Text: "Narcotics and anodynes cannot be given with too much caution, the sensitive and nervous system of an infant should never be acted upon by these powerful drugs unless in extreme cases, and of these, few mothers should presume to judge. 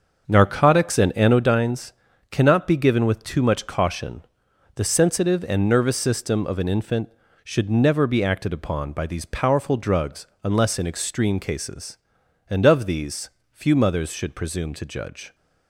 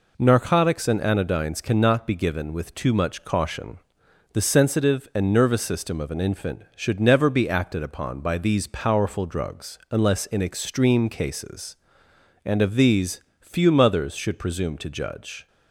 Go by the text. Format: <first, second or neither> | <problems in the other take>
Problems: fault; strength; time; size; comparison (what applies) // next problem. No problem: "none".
second | starts louder than the rest; until 1.5 s; 6.5 dB // pauses between "anodynes" and "cannot"; at 1.9 s; 0.38 s long // pauses between "drugs" and "unless"; slight; at 10.2 s; 0.18 s long